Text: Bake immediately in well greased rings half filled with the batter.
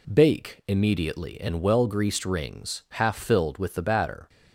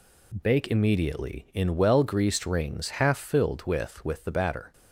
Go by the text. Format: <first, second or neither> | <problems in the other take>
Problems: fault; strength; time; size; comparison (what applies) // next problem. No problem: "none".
first | says "with" twice; at 4.0 s